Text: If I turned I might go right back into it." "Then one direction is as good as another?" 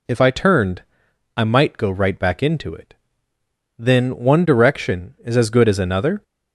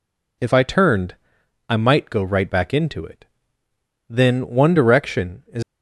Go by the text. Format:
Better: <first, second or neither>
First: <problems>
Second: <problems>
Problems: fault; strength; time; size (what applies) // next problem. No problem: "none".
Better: first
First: pauses between "turned" and "I"; noticeable; at 0.8 s; 0.54 s long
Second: pauses between "turned" and "I"; noticeable; at 1.1 s; 0.54 s long // stops before "as good as another"; at 5.6 s